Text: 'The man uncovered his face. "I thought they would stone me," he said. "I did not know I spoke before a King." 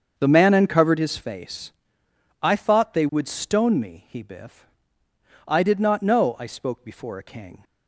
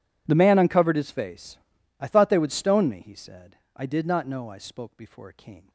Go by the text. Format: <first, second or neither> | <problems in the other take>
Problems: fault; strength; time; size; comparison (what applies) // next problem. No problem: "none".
second | starts louder than the rest; until 1.1 s; 7 dB // says "biff" for "said"; at 4.2 s